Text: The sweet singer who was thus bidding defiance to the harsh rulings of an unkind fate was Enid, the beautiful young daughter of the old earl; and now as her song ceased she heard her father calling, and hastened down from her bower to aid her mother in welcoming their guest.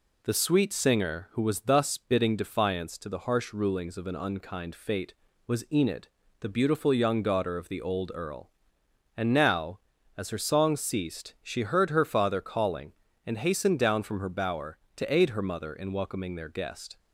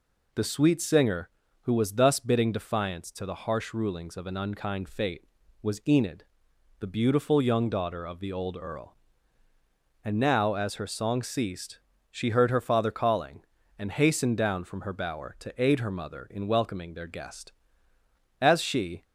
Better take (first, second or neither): first